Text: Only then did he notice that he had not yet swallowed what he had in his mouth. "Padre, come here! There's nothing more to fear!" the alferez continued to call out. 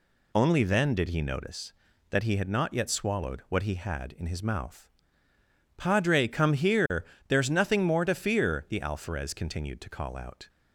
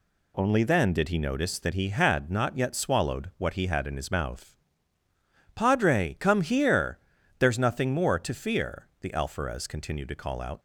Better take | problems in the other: neither | none

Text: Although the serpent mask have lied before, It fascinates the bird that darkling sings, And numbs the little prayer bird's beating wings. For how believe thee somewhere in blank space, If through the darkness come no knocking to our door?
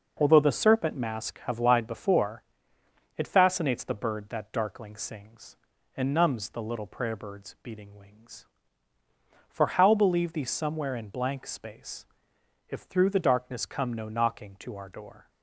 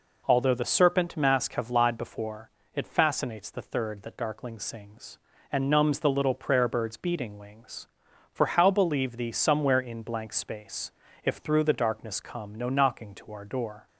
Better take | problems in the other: first | says "third" for "bird"; at 3.6 s

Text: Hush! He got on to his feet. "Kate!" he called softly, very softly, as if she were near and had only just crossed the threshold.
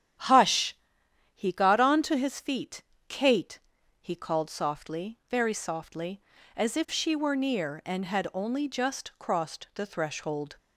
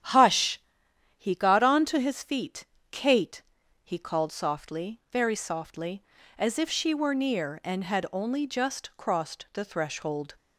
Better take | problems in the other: neither | starts louder than the rest; strong; the same in both

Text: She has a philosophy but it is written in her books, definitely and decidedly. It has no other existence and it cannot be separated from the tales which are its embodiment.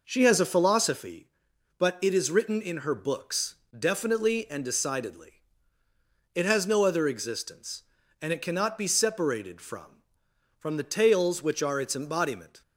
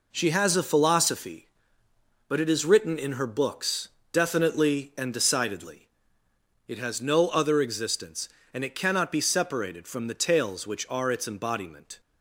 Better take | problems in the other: second | says "from" twice; at 10.5 s

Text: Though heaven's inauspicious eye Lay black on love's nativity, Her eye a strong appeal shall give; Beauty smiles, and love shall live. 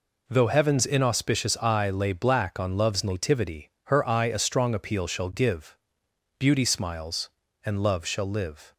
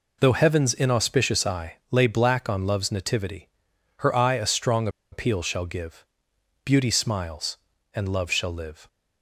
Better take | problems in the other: first | pauses between "eye" and "Lay"; slight; at 1.7 s; 0.16 s long // pauses between "strong" and "appeal"; slight; at 4.8 s; 0.23 s long

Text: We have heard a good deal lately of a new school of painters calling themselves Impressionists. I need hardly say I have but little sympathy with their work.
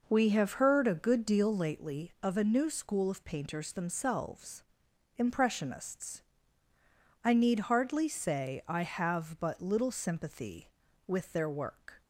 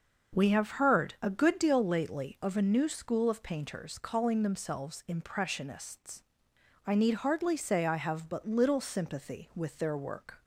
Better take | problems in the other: second | skips "calling"; at 3.7 s // pauses between "themselves" and "Impressionists"; noticeable; at 4.6 s; 0.54 s long

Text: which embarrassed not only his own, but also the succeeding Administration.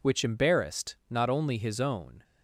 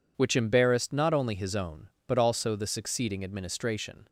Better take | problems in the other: second | stops before "but also the succeeding Administration"; at 2.2 s

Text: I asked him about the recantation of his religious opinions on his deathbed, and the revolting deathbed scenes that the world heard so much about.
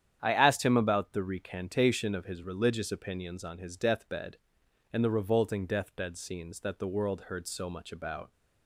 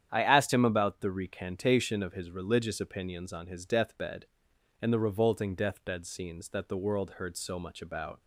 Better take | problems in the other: neither | starts louder than the rest; strong; the same in both

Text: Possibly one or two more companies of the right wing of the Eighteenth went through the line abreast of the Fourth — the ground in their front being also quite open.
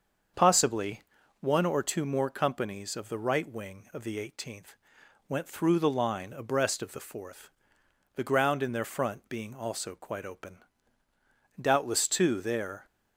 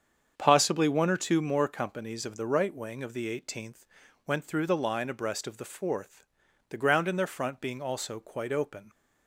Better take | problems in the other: second | starts louder than the rest; until 1.7 s; 7 dB; strong in the second // pauses between "Possibly" and "one"; at 1.0 s; 0.38 s long // pauses between "Eighteenth" and "went"; noticeable; at 4.7 s; 0.52 s long; also in the second // goes on to say "Doubtless too there"; noticeable; from 11.5 s on; 1.2 s long

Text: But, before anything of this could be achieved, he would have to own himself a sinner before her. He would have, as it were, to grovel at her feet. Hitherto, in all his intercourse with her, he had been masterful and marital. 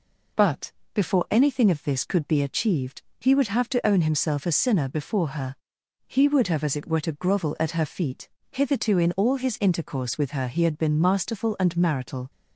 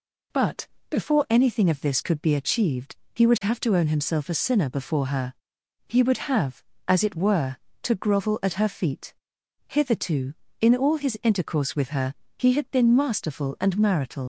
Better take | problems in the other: first | leaves "marital" unfinished; at 14.2 s; 95 ms

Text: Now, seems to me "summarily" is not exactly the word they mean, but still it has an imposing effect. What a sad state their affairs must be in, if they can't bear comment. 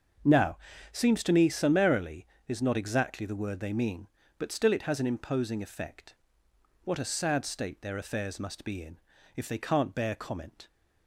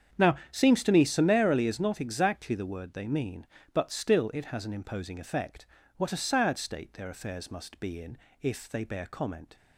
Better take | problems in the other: first | starts louder than the rest; strong; until 1.3 s; 8 dB; also in the first // skips "can't"; at 8.8 s

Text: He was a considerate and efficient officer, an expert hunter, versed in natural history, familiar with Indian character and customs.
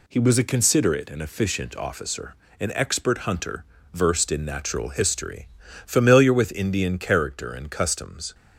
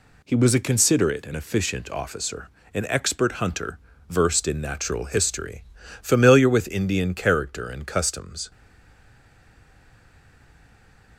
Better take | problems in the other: first | stays silent after the last word; strong; from 8.5 s on; 2.6 s long

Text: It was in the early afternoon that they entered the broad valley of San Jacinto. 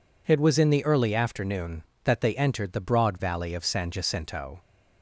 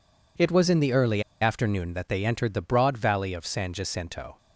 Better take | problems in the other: first | pauses between "early" and "afternoon"; slight; at 1.2 s; 0.18 s long

